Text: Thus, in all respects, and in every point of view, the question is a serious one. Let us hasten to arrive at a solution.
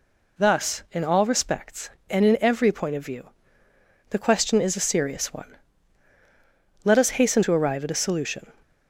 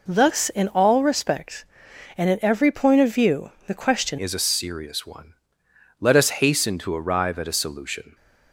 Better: first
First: none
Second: changes voice at "is"; from 4.1 s on; 4.0 s long

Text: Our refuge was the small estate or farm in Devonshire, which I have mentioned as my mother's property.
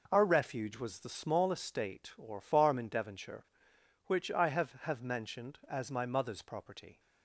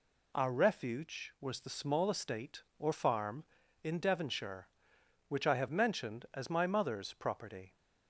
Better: second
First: says "have" twice; at 4.8 s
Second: none

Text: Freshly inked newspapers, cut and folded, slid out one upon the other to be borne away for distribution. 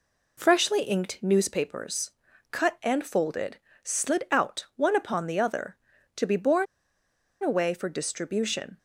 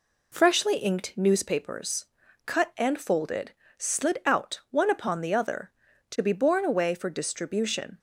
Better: second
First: pauses between "borne" and "away"; noticeable; at 6.6 s; 0.78 s long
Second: none

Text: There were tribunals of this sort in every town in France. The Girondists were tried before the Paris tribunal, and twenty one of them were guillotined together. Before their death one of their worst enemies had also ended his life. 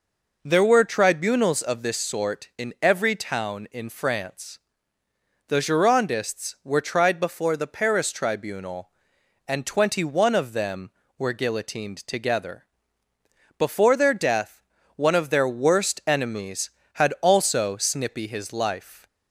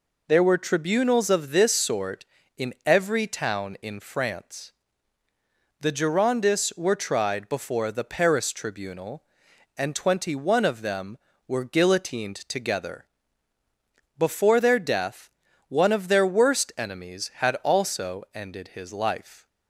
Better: second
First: pauses between "death" and "one"; slight; at 14.6 s; 0.34 s long // says "snippy" for "ended"; at 17.7 s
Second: pauses between "death" and "one"; at 15.2 s; 0.38 s long

